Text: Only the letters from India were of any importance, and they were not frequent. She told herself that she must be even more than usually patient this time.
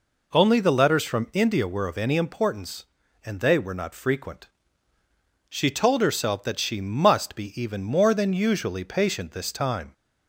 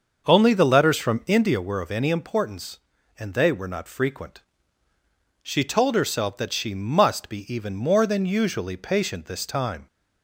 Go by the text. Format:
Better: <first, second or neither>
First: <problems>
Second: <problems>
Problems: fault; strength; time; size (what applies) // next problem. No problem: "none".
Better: first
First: none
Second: starts louder than the rest; until 1.6 s; 6.5 dB